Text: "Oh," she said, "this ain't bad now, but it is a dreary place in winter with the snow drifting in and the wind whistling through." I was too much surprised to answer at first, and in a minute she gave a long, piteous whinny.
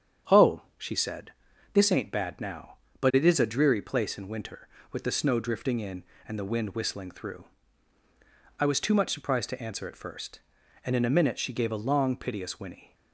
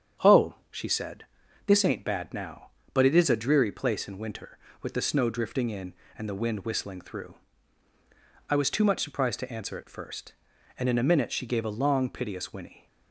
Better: neither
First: starts louder than the rest; strong; until 1.8 s; 8 dB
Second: starts louder than the rest; strong; until 1.8 s; 8 dB

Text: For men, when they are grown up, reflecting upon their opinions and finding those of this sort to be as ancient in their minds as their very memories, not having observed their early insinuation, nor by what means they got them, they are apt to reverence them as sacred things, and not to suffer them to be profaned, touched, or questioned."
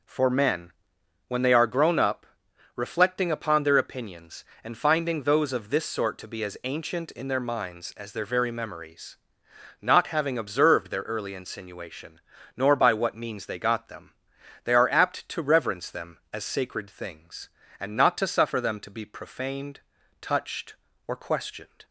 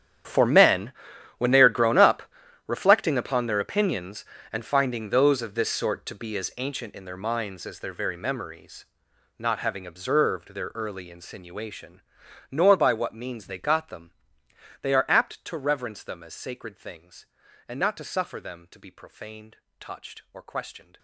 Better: first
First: none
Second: gets quieter; strong; throughout; 17.5 dB

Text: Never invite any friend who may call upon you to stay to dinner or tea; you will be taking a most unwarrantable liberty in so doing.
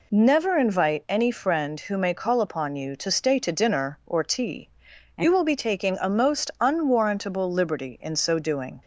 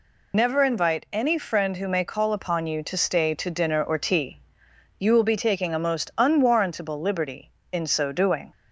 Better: first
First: none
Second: loses the start of "Never"; at 0.3 s; 75 ms

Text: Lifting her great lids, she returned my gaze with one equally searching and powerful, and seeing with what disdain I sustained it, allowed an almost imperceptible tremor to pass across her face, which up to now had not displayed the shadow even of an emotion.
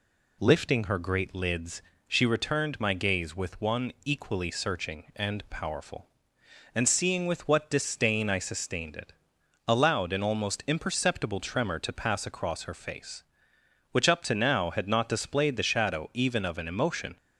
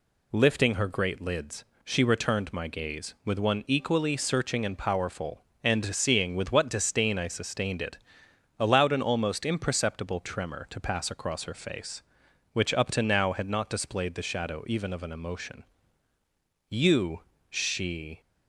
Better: first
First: none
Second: goes on to say "You she"; from 16.6 s on; 1.5 s long

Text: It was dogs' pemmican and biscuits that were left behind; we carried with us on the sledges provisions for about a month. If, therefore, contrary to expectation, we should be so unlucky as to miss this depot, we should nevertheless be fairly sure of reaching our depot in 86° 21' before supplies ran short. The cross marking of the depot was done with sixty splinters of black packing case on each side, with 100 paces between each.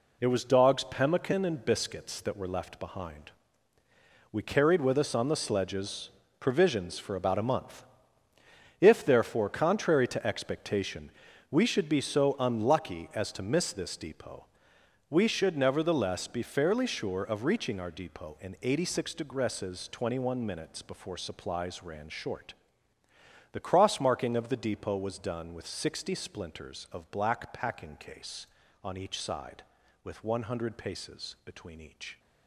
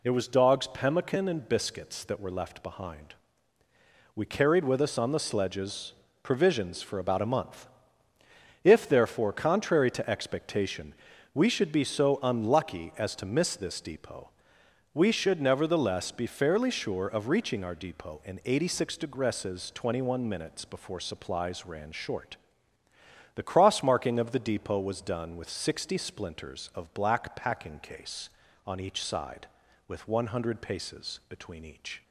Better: second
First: gets quieter; strong; throughout; 9.5 dB // pauses between "sledges" and "provisions"; slight; at 6.0 s; 0.32 s long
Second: pauses between "sledges" and "provisions"; slight; at 5.9 s; 0.32 s long

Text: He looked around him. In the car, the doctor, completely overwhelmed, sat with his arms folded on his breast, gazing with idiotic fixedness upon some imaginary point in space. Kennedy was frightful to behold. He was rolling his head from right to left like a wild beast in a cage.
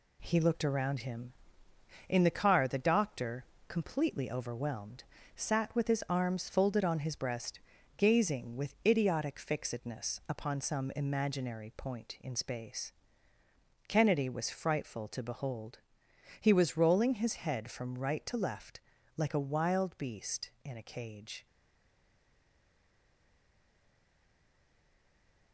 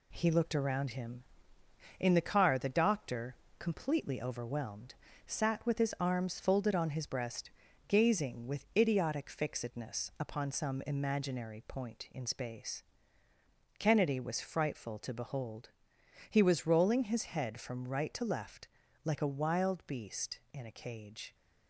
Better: second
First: pauses between "left" and "like"; at 18.7 s; 0.38 s long // stays silent after the last word; strong; from 21.4 s on; 4.1 s long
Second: pauses between "left" and "like"; at 18.6 s; 0.38 s long

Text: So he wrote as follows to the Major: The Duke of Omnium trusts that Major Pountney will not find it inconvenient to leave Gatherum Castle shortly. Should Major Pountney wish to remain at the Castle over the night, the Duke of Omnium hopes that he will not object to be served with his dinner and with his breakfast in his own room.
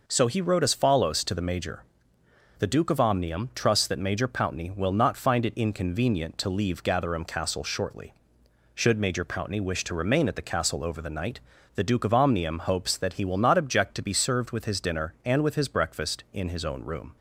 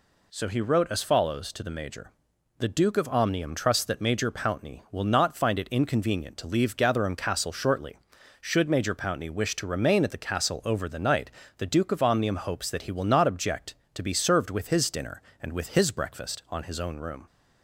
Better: first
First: none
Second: says "on" for "in"; at 16.4 s

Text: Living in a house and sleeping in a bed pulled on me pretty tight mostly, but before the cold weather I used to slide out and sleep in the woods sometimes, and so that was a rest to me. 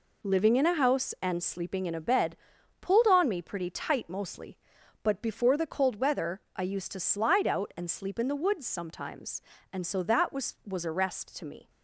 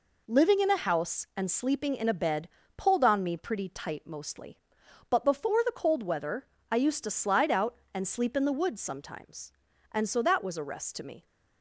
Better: second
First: pauses between "bed" and "pulled"; noticeable; at 2.3 s; 0.46 s long // pauses between "weather" and "I"; slight; at 6.4 s; 0.16 s long // says "was" twice; at 10.6 s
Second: pauses between "bed" and "pulled"; slight; at 2.4 s; 0.30 s long // pauses between "weather" and "I"; slight; at 6.4 s; 0.26 s long

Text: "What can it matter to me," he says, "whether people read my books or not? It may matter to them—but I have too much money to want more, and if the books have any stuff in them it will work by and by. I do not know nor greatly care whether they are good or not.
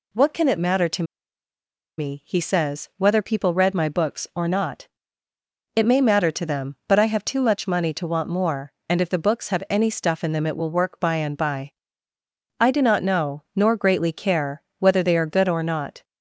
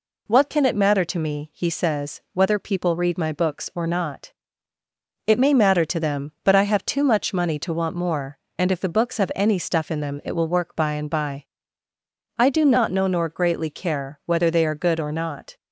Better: second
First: pauses between "to" and "me"; noticeable; at 1.0 s; 0.94 s long // pauses between "care" and "whether"; slight; at 14.6 s; 0.18 s long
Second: none

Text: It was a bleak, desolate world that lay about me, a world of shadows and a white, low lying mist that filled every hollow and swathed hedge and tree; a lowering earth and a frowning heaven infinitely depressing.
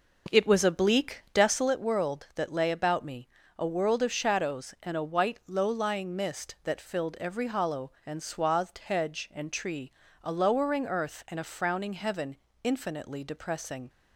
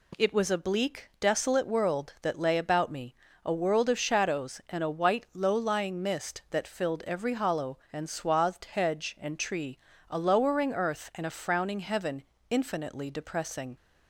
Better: second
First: starts louder than the rest; noticeable; until 1.7 s; 4.5 dB // pauses between "heaven" and "infinitely"; slight; at 12.3 s; 0.26 s long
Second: pauses between "heaven" and "infinitely"; slight; at 12.2 s; 0.26 s long

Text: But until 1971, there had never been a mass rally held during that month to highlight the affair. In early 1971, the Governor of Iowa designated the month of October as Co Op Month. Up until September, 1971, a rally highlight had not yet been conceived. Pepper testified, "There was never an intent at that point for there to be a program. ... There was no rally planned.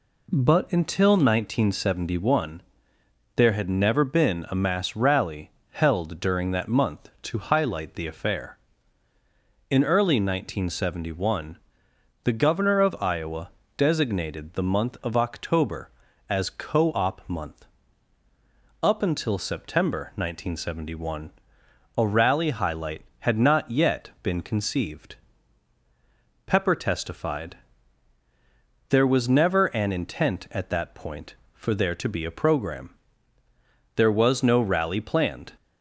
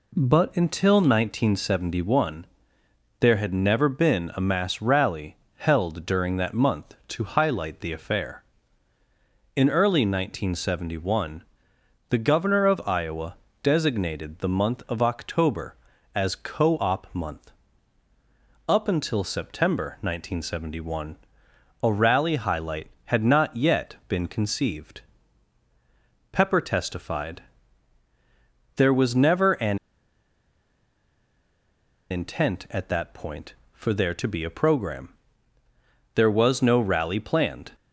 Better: first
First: pauses between "rally" and "held"; slight; at 5.5 s; 0.18 s long // pauses between "Iowa" and "designated"; slight; at 13.4 s; 0.28 s long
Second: pauses between "rally" and "held"; slight; at 5.3 s; 0.18 s long // pauses between "Iowa" and "designated"; slight; at 13.3 s; 0.28 s long // pauses between "an" and "intent"; strong; at 29.7 s; 2.3 s long

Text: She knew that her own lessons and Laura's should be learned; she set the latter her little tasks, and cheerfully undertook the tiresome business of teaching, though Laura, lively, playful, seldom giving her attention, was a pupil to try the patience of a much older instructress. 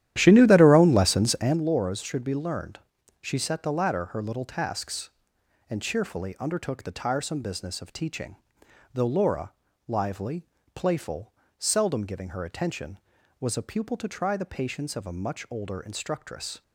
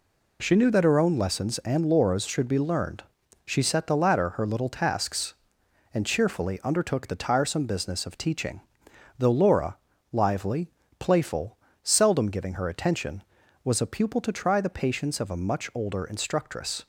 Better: second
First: starts louder than the rest; strong; until 1.7 s; 12 dB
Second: none

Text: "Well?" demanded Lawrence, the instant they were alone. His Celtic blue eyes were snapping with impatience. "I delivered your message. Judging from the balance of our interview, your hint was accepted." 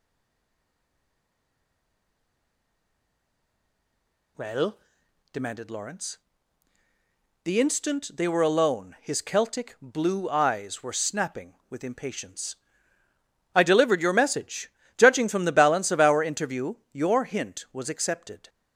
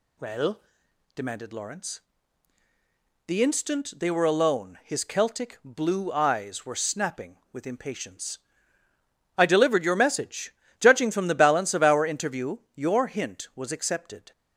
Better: second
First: stays silent before the first word; strong; until 4.3 s; 4.3 s long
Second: none

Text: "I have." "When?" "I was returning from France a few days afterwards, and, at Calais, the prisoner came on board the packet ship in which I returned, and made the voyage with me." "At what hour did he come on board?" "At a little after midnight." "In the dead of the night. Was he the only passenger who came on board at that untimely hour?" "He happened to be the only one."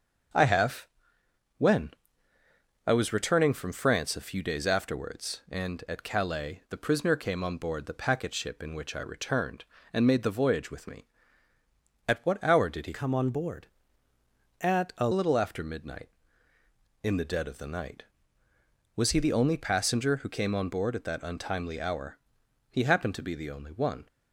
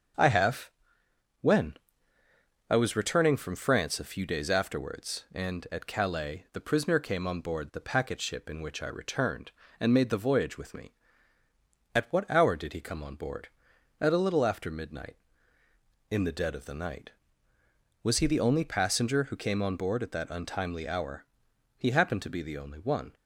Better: second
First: starts louder than the rest; strong; until 2.9 s; 7.5 dB // changes voice from "come" to "a"; from 12.9 to 15.0 s; 2.1 s long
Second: starts louder than the rest; strong; until 2.8 s; 7.5 dB

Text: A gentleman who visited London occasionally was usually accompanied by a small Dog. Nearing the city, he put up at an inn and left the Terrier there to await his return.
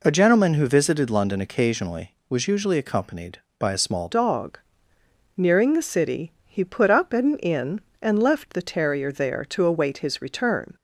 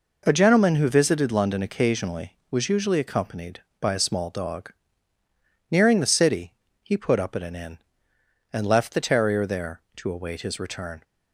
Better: second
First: changes voice at "Dog"; from 4.1 s on; 6.6 s long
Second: none

